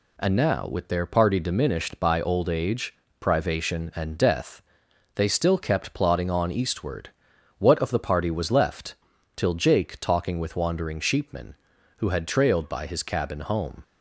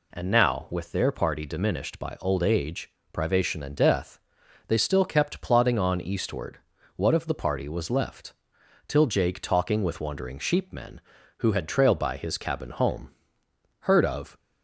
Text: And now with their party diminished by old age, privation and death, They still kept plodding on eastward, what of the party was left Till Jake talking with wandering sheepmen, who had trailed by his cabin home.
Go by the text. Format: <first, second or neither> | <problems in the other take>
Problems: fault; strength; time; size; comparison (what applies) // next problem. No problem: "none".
first | pauses between "left" and "Till"; noticeable; at 8.3 s; 0.54 s long; also in the first // goes on to say "Heard of"; from 13.8 s on; 0.56 s long